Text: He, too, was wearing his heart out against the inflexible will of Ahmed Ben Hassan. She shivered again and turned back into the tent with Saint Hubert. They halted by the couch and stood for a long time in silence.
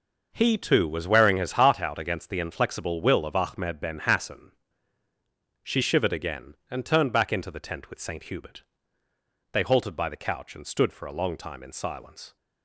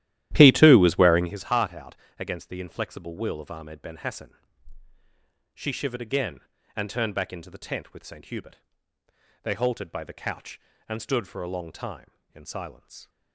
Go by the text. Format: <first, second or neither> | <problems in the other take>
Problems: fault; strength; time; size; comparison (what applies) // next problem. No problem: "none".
first | starts louder than the rest; strong; until 1.4 s; 13 dB // pauses between "out" and "against"; slight; at 1.9 s; 0.24 s long